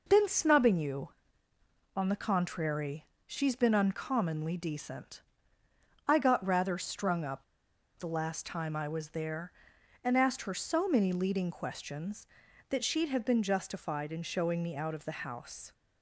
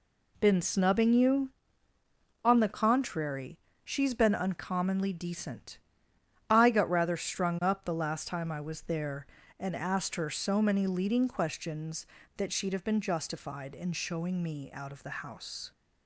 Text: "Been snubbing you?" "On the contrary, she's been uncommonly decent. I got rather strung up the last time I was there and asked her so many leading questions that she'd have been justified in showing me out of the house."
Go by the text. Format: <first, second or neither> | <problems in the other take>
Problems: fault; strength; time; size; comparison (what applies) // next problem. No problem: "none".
second | pauses between "up" and "the"; noticeable; at 7.4 s; 0.56 s long